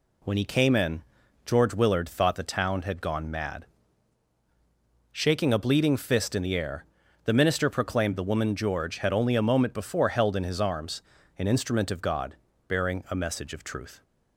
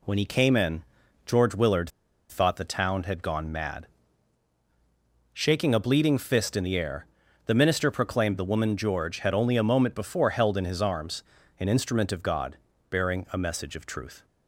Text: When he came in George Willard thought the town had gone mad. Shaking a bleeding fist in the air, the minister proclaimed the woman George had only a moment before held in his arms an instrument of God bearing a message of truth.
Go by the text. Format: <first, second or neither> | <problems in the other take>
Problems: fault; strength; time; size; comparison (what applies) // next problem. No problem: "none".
first | pauses between "in" and "George"; at 0.8 s; 0.42 s long; also in the first // pauses between "Willard" and "thought"; at 1.8 s; 0.42 s long // pauses between "arms" and "an"; at 11.2 s; 0.38 s long; also in the first // pauses between "God" and "bearing"; slight; at 12.5 s; 0.34 s long; slight in the first